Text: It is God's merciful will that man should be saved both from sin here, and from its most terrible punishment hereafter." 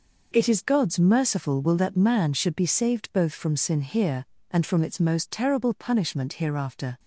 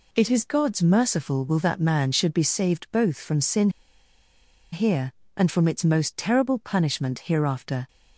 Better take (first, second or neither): first